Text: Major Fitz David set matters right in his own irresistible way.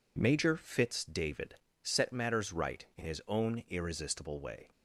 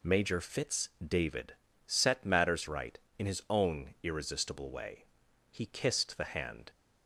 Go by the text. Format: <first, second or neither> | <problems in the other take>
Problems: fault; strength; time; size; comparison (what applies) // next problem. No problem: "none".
first | pauses between "Fitz" and "David"; slight; at 0.8 s; 0.16 s long // pauses between "David" and "set"; slight; at 1.5 s; 0.32 s long; slight in the first // goes on to say "He kissed the hand"; noticeable; from 5.5 s on; 1.1 s long